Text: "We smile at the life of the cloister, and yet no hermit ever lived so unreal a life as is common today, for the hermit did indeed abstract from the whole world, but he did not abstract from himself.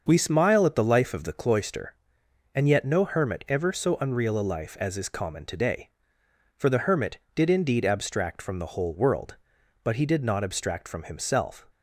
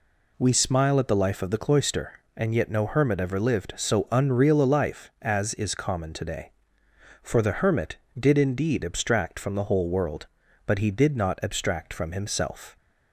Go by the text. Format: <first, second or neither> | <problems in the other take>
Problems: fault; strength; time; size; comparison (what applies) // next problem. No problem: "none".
second | starts louder than the rest; until 1.0 s; 6.5 dB // skips "lived"; at 3.7 s